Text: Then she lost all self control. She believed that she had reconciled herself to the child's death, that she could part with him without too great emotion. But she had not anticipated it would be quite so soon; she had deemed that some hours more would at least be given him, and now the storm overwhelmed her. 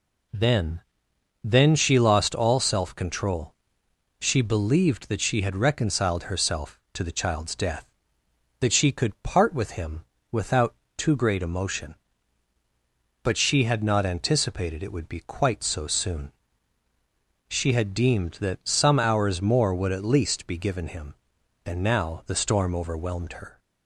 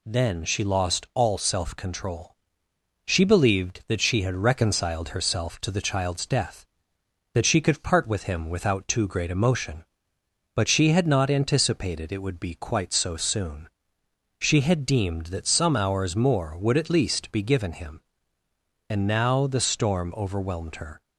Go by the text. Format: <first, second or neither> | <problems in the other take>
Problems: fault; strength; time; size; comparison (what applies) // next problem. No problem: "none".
second | says "Then" twice; at 1.4 s // pauses between "him" and "without"; slight; at 10.0 s; 0.26 s long // pauses between "without" and "too"; slight; at 10.7 s; 0.24 s long